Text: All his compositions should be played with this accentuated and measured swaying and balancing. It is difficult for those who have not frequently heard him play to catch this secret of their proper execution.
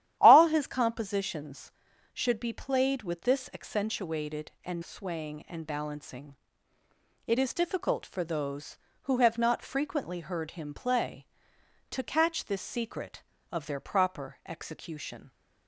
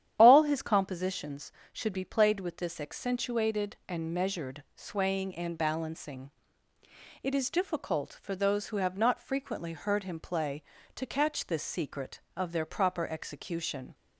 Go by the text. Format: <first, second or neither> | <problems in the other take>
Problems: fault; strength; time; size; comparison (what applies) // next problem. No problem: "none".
second | starts louder than the rest; strong; until 1.2 s; 11.5 dB; strong in the second // skips "measured"; at 4.8 s